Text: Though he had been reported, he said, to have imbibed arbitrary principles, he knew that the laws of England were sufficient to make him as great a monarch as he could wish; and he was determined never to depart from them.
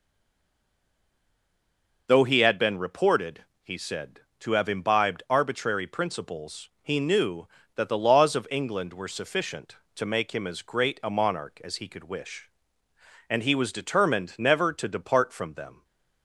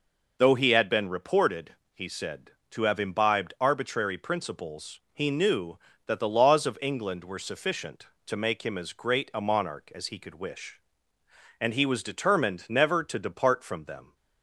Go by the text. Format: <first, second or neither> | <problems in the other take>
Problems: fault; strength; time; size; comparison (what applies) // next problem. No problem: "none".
second | stays silent before the first word; noticeable; until 2.0 s; 2.0 s long